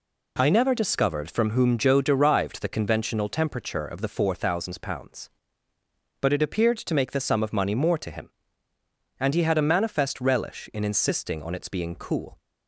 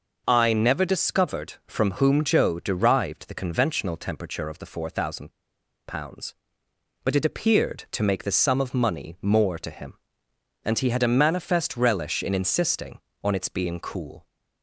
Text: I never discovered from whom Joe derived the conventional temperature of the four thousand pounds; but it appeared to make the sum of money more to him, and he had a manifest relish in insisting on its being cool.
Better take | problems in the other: first | pauses between "thousand" and "pounds"; noticeable; at 5.3 s; 0.55 s long

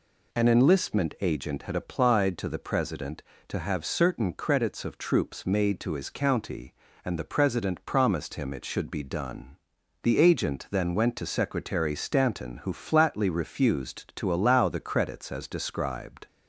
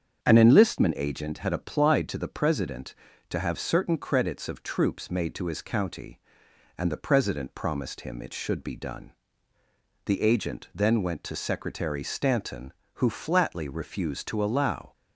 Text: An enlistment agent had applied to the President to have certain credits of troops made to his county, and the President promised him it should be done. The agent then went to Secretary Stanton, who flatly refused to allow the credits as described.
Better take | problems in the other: first | starts louder than the rest; strong; until 1.2 s; 7.5 dB // stops before "the credits as described"; at 14.9 s

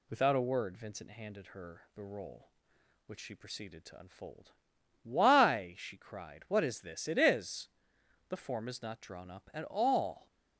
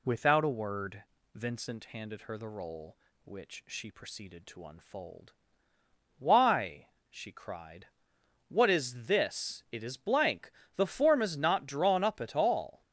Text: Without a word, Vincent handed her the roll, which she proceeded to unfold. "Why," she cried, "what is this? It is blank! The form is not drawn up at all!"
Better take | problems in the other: second | skips "blank"; at 7.9 s

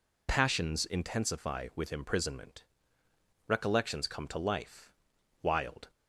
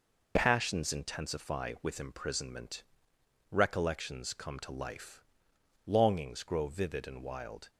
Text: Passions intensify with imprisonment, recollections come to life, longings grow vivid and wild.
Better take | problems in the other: second | skips "longings grow vivid and"; at 5.1 s

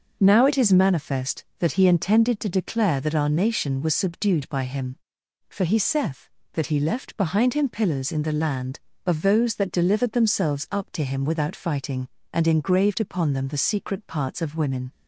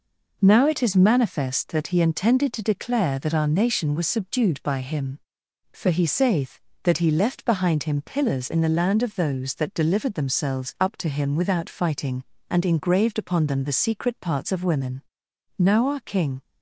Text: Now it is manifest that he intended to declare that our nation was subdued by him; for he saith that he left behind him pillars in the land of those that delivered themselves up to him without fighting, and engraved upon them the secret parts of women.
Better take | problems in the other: first | goes on to say "Now our king"; noticeable; from 15.5 s on; 0.82 s long

